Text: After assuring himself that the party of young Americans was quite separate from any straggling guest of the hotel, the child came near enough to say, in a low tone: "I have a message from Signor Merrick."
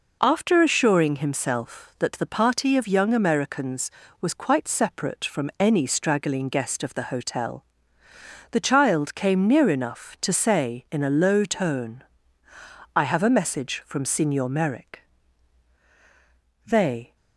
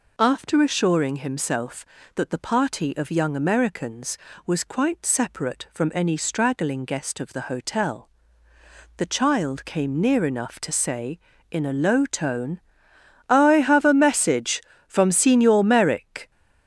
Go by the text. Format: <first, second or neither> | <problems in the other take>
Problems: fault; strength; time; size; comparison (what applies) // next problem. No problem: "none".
second | goes on to say "They"; from 16.6 s on; 0.50 s long